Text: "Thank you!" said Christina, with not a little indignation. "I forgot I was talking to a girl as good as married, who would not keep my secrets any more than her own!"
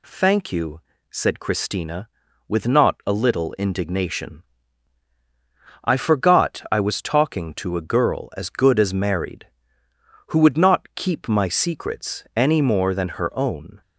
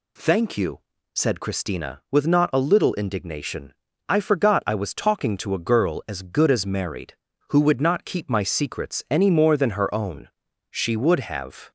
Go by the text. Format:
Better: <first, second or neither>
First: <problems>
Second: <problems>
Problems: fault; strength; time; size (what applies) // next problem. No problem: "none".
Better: first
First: none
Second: goes on to say "She would have"; noticeable; from 10.7 s on; 1.0 s long